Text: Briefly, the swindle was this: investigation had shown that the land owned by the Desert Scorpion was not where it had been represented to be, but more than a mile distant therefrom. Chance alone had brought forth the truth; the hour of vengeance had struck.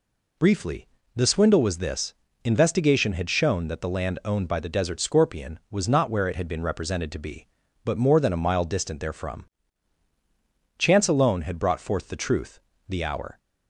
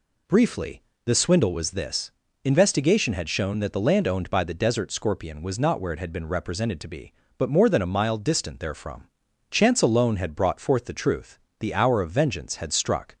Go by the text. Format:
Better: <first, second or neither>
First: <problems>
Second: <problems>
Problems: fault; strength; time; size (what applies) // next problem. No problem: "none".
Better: second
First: stops before "of vengeance had struck"; at 13.3 s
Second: none